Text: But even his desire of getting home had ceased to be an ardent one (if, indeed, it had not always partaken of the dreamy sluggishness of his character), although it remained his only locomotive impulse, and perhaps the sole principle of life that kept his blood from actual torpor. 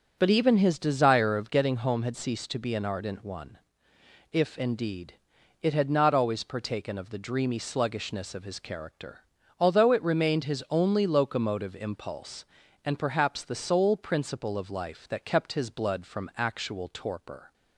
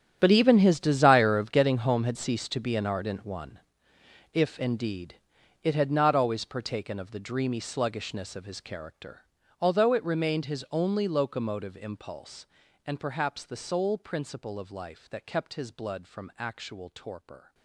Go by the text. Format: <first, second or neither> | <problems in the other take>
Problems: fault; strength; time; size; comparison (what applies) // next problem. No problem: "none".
first | gets quieter; strong; throughout; 16.5 dB